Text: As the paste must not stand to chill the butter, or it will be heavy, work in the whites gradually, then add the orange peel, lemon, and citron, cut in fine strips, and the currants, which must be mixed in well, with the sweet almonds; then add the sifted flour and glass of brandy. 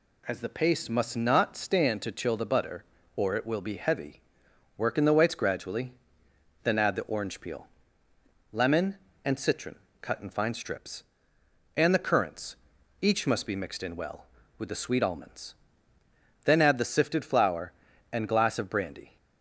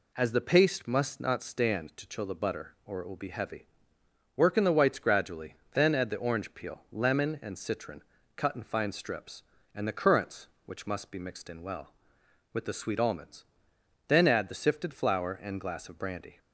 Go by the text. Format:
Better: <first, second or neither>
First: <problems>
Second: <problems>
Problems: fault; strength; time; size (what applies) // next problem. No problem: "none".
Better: second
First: says "each" for "which"; at 13.0 s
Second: none